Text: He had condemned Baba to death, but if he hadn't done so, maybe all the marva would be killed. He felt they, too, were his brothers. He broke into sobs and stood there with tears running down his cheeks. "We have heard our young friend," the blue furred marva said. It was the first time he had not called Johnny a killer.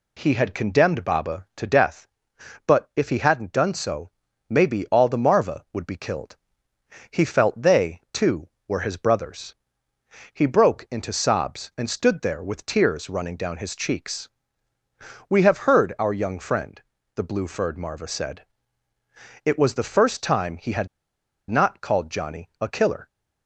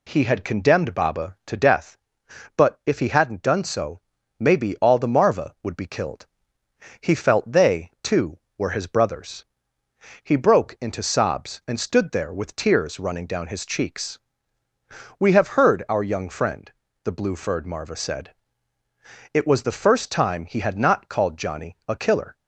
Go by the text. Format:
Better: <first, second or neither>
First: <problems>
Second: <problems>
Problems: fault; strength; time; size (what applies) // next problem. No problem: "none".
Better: second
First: pauses between "had" and "not"; noticeable; at 20.8 s; 0.62 s long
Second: none